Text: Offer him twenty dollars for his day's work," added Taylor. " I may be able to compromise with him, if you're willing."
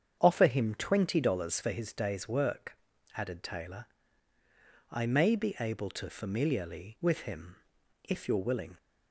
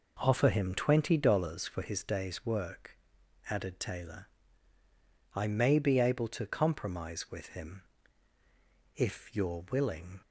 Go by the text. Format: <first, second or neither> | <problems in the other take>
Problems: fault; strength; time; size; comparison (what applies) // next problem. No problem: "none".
second | starts louder than the rest; strong; until 1.2 s; 8.5 dB // says "familiarly" for "compromise"; at 6.0 s